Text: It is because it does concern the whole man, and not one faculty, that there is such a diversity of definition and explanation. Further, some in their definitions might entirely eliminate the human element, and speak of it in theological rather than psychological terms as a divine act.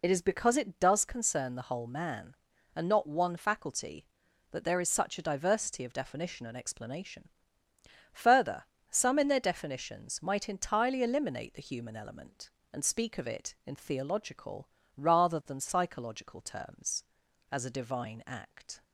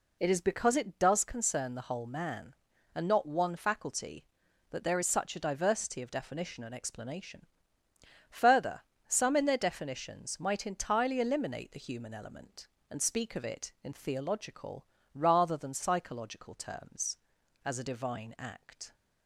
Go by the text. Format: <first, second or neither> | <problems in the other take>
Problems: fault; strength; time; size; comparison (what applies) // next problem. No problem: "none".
second | loses the start of "It"; at 0.0 s; 30 ms // pauses between "theological" and "rather"; slight; at 14.6 s; 0.30 s long; slight in the second